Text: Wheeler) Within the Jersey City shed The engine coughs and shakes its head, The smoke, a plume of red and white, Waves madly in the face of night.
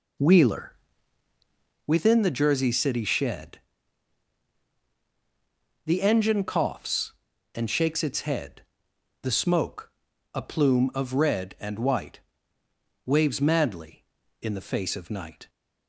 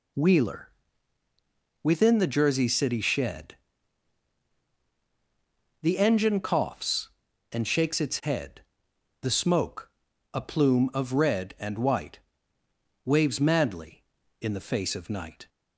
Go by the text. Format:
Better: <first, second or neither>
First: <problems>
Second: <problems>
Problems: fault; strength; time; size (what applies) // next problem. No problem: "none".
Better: second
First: starts louder than the rest; slight; until 1.9 s; 3.5 dB // pauses between "shed" and "The"; strong; at 3.5 s; 2.2 s long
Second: pauses between "shed" and "The"; strong; at 3.5 s; 2.2 s long